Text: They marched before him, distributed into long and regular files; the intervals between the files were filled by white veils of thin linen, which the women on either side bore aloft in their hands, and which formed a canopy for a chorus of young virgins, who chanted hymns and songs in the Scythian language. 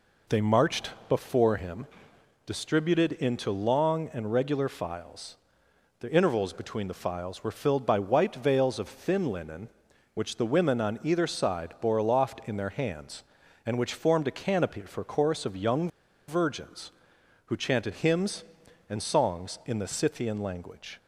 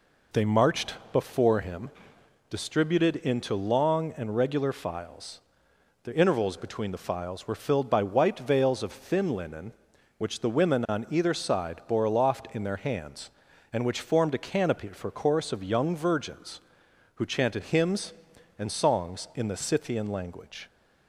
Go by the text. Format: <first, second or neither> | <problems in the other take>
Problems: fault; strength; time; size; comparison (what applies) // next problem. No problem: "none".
second | pauses between "marched" and "before"; slight; at 0.9 s; 0.18 s long; slight in the second // pauses between "young" and "virgins"; at 15.8 s; 0.39 s long